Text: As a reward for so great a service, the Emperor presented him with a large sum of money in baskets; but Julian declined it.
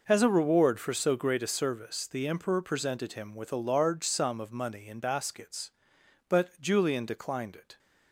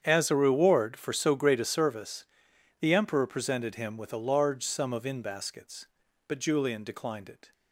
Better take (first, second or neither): first